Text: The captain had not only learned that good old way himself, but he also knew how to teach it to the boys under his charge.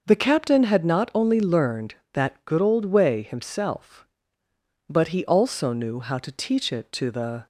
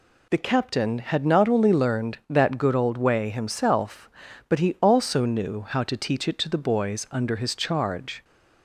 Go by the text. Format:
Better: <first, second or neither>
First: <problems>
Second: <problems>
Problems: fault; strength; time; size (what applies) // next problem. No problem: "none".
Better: second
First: starts louder than the rest; noticeable; until 1.0 s; 6 dB // stops before "boys under his charge"; at 7.4 s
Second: none